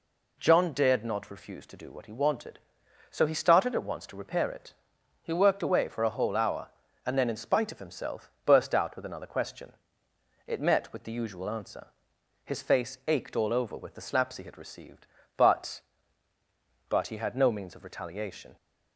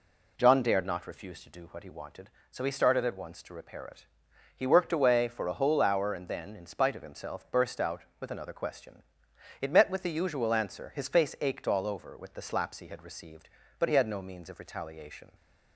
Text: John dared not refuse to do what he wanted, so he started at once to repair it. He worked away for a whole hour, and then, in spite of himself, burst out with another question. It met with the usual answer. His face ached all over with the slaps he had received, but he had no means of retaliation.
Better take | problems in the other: second | says "but" twice; at 16.8 s

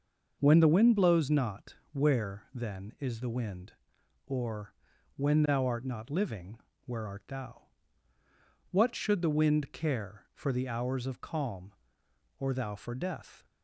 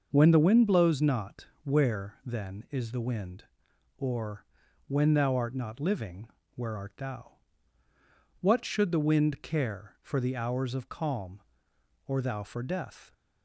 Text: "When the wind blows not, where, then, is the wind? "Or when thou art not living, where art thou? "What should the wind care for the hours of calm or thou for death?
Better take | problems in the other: neither | starts louder than the rest; the same in both // pauses between "Or" and "when"; the same in both

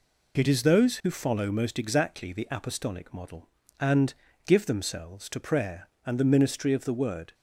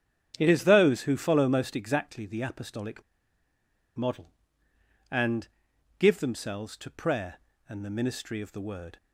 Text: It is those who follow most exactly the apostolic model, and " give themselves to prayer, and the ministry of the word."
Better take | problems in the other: first | starts louder than the rest; strong; until 1.3 s; 9 dB // pauses between "apostolic" and "model"; noticeable; at 3.0 s; 0.96 s long

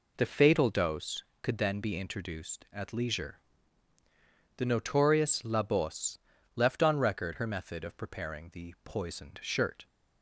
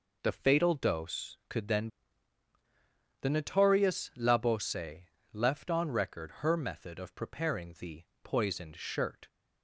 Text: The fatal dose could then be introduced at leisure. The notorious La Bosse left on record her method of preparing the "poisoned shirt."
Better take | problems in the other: first | skips "be introduced at leisure"; at 2.5 s // pauses between "Bosse" and "left"; slight; at 5.0 s; 0.28 s long; slight in the first // pauses between "the" and "poisoned"; slight; at 8.0 s; 0.22 s long

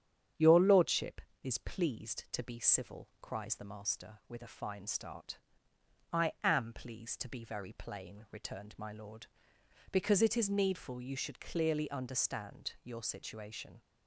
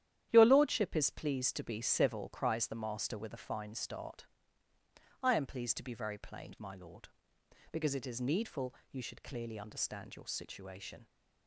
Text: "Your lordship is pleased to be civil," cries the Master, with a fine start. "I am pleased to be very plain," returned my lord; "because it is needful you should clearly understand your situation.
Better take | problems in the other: first | starts louder than the rest; strong; until 1.3 s; 11 dB; strong in the first // skips "returned"; at 6.5 s // pauses between "needful" and "you"; slight; at 8.7 s; 0.16 s long

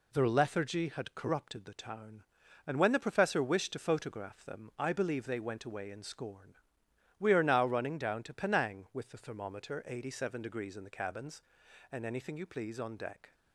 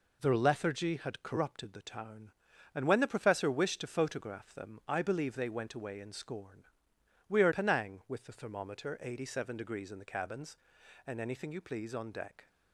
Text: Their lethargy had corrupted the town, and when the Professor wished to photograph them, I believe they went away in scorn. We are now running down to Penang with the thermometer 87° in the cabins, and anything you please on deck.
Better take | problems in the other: first | skips "now running down to"; at 7.5 s

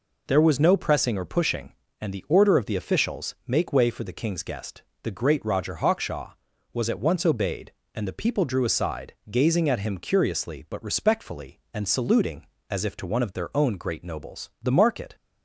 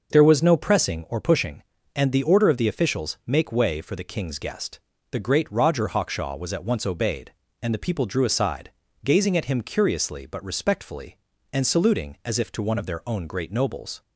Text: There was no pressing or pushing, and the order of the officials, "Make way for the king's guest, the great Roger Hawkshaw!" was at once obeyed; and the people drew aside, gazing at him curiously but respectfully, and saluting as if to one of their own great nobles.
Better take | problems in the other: second | goes on to say "The market"; from 14.6 s on; 0.54 s long

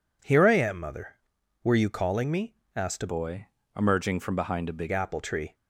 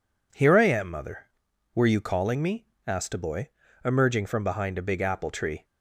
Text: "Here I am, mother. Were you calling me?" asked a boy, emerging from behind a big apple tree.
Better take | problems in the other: second | changes voice from "boy" to "big"; from 3.0 to 4.9 s; 1.9 s long

